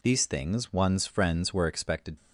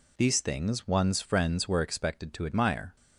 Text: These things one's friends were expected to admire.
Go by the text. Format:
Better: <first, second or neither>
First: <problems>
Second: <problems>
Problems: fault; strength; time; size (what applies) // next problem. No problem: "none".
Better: second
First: stops before "to admire"; at 2.1 s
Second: none